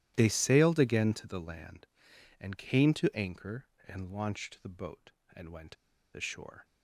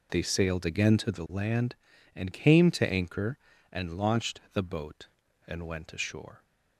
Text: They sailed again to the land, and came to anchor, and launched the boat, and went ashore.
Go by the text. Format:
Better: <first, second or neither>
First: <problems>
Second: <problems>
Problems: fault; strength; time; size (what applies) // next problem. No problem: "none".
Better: second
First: starts louder than the rest; strong; until 1.1 s; 13 dB // pauses between "went" and "ashore"; at 5.7 s; 0.39 s long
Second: none